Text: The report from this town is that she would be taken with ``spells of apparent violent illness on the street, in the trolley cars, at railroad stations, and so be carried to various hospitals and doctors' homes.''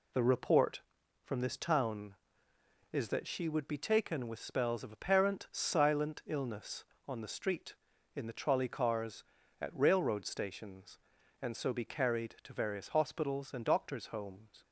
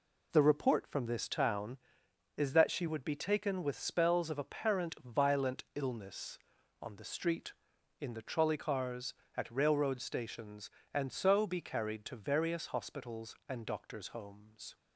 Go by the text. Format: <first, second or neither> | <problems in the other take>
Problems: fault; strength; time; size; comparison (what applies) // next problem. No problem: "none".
second | says "silent" for "violent"; at 5.5 s